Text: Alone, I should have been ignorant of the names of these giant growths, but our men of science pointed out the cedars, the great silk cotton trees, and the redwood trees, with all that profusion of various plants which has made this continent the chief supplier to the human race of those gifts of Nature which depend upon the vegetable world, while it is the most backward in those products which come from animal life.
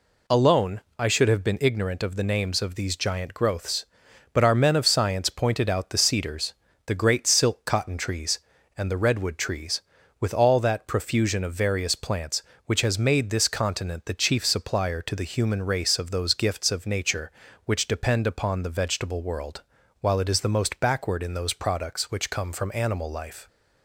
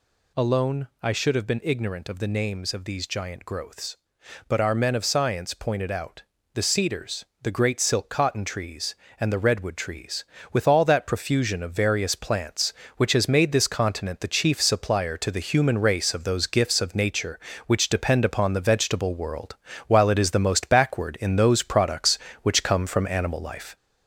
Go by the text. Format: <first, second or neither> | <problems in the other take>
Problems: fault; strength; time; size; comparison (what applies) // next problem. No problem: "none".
first | gets louder; noticeable; throughout; 4 dB // pauses between "out" and "the"; slight; at 6.2 s; 0.32 s long